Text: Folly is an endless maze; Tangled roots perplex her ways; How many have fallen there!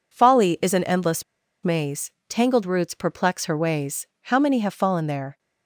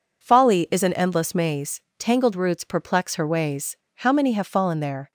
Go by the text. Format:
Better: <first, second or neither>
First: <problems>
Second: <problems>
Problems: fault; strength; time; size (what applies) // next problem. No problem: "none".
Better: second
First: pauses between "endless" and "maze"; at 1.2 s; 0.40 s long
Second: none